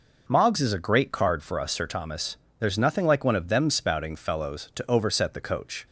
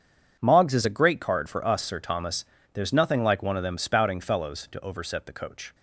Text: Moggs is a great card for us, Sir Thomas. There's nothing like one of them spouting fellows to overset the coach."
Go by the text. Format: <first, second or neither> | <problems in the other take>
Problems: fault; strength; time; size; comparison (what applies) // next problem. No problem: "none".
neither | none